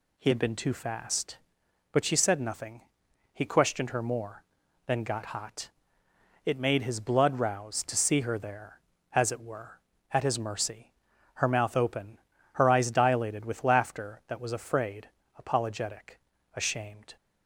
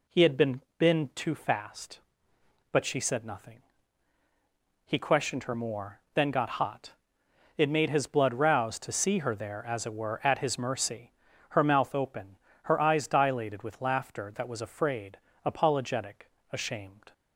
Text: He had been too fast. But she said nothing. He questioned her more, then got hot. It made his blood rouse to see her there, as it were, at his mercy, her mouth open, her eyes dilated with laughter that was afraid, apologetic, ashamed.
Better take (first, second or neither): first